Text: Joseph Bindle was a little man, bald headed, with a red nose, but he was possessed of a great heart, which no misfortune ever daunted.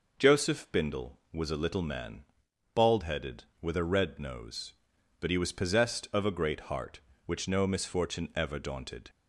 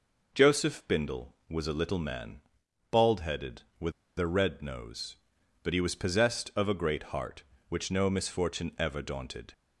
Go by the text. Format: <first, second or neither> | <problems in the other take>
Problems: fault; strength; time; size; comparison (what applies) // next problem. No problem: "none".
first | pauses between "with" and "a"; slight; at 3.9 s; 0.26 s long